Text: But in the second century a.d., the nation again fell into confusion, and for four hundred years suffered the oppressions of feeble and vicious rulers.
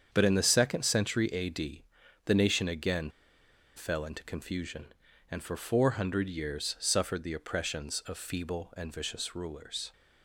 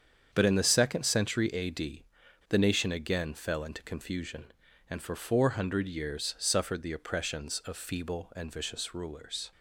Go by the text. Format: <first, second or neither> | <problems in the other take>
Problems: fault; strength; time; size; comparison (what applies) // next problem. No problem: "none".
second | starts louder than the rest; strong; until 1.1 s; 7.5 dB; strong in the second // pauses between "again" and "fell"; noticeable; at 3.0 s; 0.66 s long